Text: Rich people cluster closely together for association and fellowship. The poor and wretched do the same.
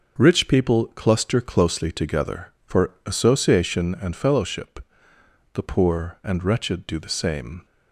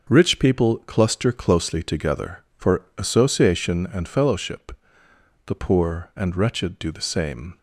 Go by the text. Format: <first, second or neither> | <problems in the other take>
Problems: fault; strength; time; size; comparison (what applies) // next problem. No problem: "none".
neither | none